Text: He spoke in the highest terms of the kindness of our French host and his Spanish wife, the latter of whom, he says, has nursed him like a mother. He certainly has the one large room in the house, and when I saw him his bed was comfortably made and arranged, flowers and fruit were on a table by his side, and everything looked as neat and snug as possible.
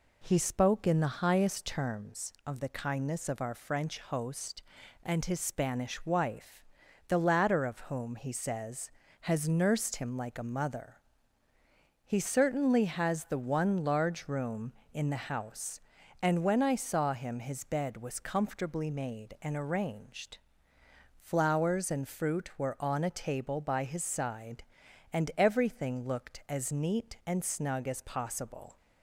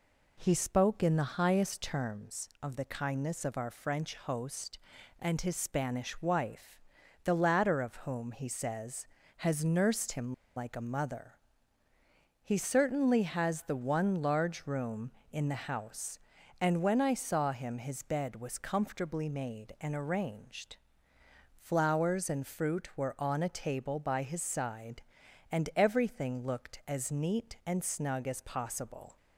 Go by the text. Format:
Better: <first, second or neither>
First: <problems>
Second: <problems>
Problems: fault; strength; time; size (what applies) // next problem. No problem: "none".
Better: first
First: none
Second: pauses between "him" and "like"; slight; at 10.3 s; 0.23 s long